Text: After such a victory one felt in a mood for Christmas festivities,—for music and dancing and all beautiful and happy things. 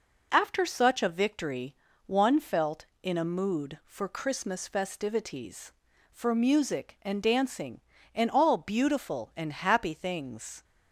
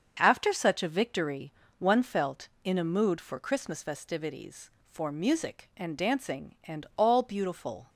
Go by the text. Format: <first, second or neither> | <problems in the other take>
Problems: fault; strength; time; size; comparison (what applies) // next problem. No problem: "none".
first | starts louder than the rest; until 1.2 s; 7 dB // pauses between "victory" and "one"; slight; at 1.5 s; 0.26 s long; slight in the first // stops before "and happy things"; at 7.8 s